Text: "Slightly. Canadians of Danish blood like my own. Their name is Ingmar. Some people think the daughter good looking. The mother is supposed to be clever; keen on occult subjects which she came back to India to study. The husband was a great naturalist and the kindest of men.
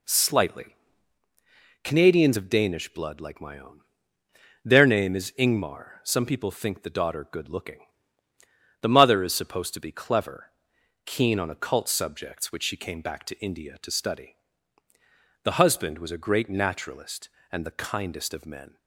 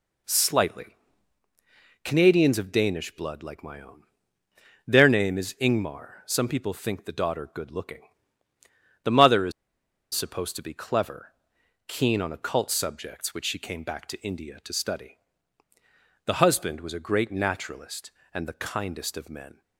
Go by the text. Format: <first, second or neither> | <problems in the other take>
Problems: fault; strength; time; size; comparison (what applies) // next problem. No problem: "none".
first | pauses between "is" and "supposed"; noticeable; at 9.5 s; 0.62 s long